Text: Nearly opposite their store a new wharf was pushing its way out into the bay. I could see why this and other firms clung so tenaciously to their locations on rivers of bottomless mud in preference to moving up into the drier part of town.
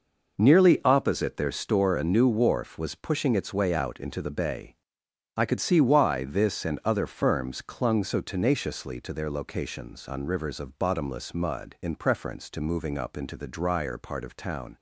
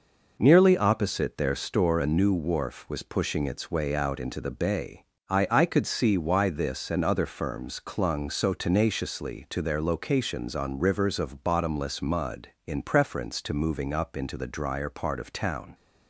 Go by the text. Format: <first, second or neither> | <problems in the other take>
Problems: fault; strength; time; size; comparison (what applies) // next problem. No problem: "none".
first | says "I" twice; at 5.5 s